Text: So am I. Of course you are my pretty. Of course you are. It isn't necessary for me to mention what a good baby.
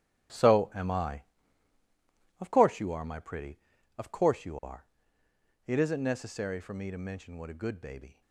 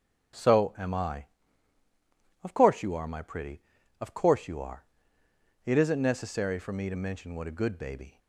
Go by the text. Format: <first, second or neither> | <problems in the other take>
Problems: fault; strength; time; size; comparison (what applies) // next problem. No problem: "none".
second | gets quieter; strong; throughout; 11.5 dB // starts louder than the rest; strong; until 2.4 s; 10 dB; noticeable in the second